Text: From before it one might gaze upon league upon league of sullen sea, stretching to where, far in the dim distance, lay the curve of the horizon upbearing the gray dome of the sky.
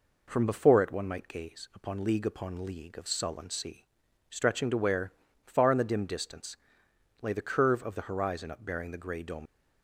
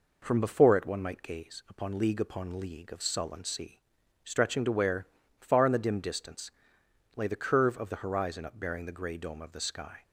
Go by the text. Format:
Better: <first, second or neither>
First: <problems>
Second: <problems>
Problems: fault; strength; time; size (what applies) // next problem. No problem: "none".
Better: second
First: stops before "of the sky"; at 9.4 s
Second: none